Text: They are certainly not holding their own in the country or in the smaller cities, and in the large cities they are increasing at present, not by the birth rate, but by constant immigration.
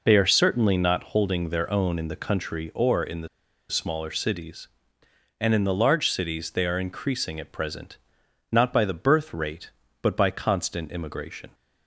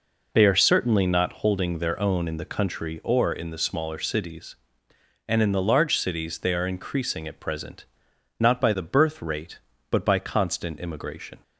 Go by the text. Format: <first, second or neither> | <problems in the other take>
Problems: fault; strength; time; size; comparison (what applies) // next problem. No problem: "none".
second | pauses between "the" and "smaller"; at 3.2 s; 0.41 s long